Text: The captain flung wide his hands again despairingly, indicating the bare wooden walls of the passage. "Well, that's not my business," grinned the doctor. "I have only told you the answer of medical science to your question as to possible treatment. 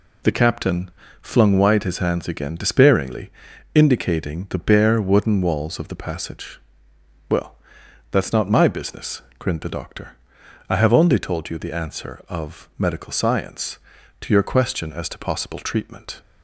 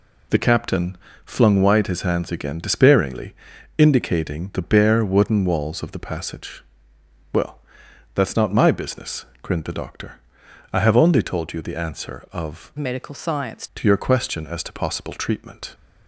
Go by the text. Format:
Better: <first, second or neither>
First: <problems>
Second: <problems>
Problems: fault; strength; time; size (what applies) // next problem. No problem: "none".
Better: first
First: pauses between "captain" and "flung"; slight; at 0.9 s; 0.31 s long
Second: pauses between "captain" and "flung"; slight; at 0.9 s; 0.28 s long // changes voice from "medical" to "science"; from 12.7 to 13.6 s; 0.9 s long